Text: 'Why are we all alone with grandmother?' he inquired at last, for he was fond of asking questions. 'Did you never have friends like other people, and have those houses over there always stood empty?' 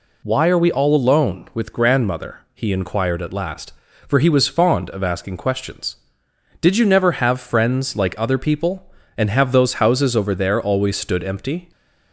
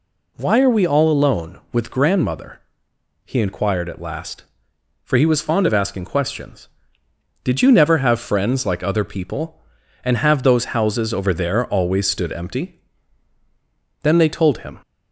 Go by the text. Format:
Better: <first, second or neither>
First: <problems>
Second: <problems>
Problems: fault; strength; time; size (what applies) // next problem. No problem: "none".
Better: first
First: none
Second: goes on to say "Then they told him"; noticeable; from 14.0 s on; 0.78 s long